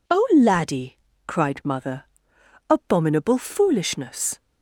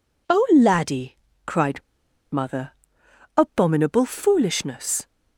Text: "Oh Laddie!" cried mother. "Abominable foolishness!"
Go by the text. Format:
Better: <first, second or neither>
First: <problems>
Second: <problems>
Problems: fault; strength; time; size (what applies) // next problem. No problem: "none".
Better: first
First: none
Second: pauses between "cried" and "mother"; noticeable; at 1.8 s; 0.52 s long